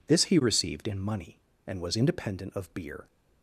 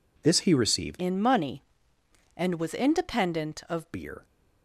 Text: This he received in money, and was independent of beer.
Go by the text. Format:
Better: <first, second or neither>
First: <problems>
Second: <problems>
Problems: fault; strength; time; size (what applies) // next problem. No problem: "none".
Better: first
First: none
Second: changes voice from "in" to "of"; from 0.9 to 3.9 s; 3.0 s long